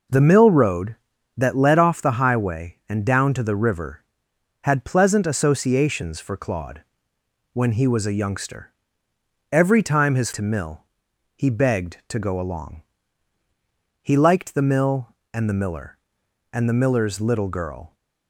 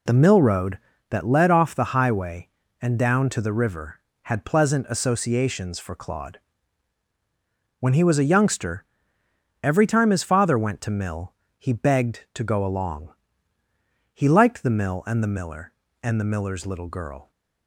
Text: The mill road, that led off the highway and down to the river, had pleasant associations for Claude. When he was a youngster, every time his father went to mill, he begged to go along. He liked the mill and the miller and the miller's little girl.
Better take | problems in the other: second | skips "father went"; at 10.3 s

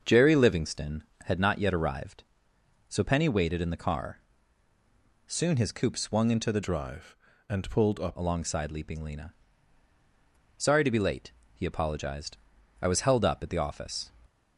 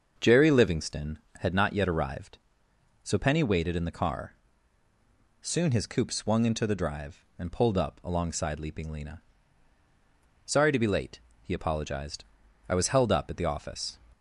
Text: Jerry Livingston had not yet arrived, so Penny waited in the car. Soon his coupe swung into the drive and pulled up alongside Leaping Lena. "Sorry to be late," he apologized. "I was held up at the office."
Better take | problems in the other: second | starts louder than the rest; until 1.0 s; 6.5 dB; also in the second // changes voice from "drive" to "up"; from 6.6 to 8.1 s; 1.5 s long

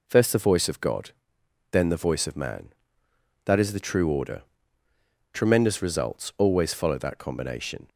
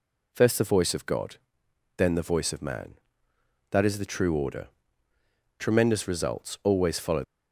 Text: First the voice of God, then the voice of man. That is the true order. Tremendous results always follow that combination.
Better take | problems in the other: first | stops before "that combination"; at 7.2 s

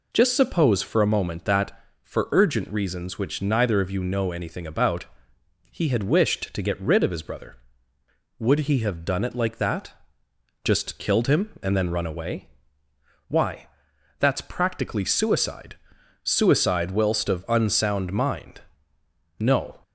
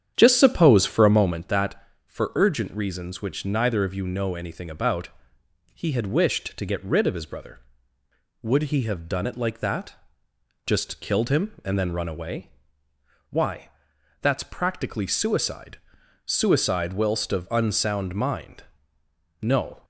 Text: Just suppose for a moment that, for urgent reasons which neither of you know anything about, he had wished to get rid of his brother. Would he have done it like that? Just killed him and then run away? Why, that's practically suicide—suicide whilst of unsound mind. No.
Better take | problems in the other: first | starts louder than the rest; strong; until 1.5 s; 9 dB

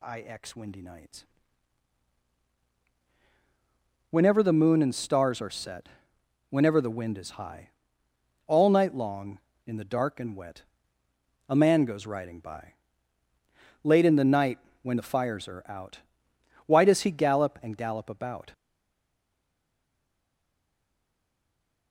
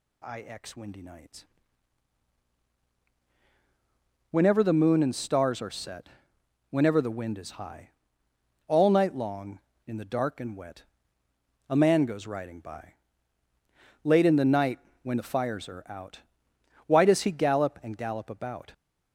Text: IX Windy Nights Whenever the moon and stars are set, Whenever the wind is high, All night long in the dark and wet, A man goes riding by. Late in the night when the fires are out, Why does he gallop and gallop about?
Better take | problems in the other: second | pauses between "Nights" and "Whenever"; strong; at 1.2 s; 2.8 s long; strong in the second // pauses between "night" and "when"; slight; at 14.5 s; 0.24 s long; slight in the second // stays silent after the last word; strong; from 18.5 s on; 3.4 s long

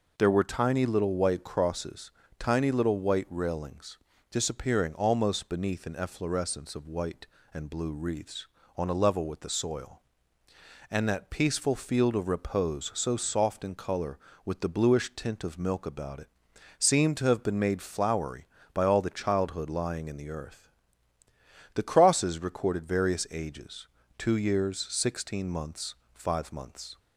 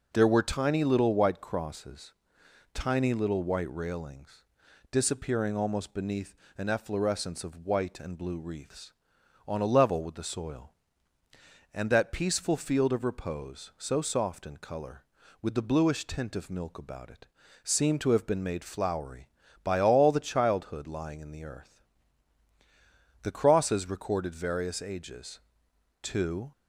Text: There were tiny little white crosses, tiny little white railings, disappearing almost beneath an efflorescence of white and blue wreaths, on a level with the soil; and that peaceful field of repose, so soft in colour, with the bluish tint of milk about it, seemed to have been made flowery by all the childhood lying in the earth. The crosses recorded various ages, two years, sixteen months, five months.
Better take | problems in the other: first | pauses between "beneath" and "an"; slight; at 6.3 s; 0.22 s long // stops before "years sixteen months five months"; at 26.5 s

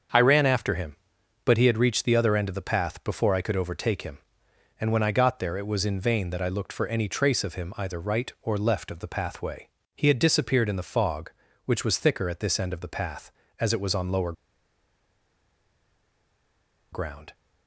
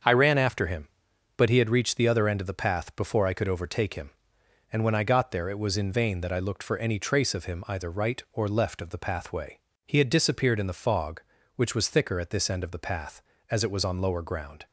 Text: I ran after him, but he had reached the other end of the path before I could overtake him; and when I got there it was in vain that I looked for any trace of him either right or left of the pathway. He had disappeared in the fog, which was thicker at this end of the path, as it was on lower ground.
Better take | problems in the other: second | starts louder than the rest; until 1.6 s; 7 dB; also in the second // pauses between "lower" and "ground"; strong; at 14.3 s; 2.5 s long

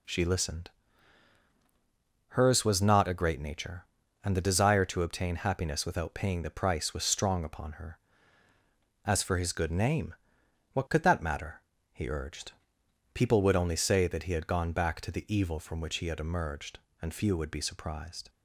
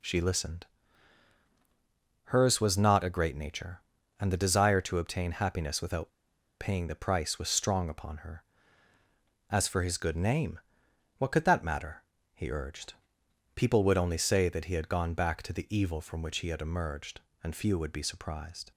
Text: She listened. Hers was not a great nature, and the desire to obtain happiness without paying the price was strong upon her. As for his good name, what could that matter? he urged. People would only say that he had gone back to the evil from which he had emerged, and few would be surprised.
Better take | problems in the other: first | pauses between "without" and "paying"; noticeable; at 6.0 s; 0.49 s long

